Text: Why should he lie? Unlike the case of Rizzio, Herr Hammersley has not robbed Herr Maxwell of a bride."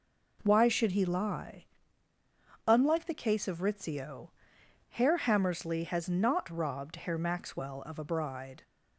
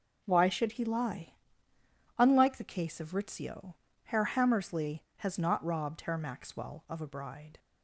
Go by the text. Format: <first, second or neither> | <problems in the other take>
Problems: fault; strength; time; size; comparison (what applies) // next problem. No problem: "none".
neither | none